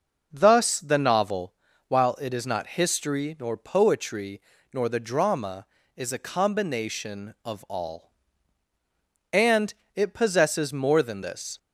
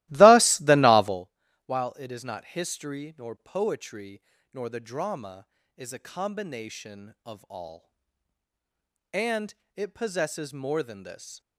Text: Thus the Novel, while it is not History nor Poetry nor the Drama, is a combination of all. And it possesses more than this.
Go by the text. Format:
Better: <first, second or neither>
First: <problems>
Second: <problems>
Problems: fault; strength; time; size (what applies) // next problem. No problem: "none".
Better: first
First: pauses between "Poetry" and "nor"; slight; at 4.3 s; 0.32 s long // pauses between "And" and "it"; slight; at 9.7 s; 0.22 s long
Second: starts louder than the rest; strong; until 1.2 s; 17.5 dB // pauses between "Poetry" and "nor"; slight; at 4.1 s; 0.32 s long // pauses between "And" and "it"; slight; at 9.5 s; 0.22 s long